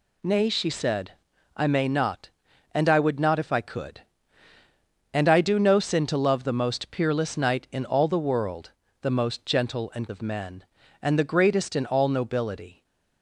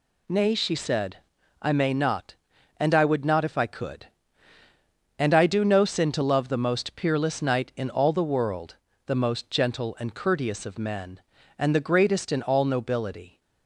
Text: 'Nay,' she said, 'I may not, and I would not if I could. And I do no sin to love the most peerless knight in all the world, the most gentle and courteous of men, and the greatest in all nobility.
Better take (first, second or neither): second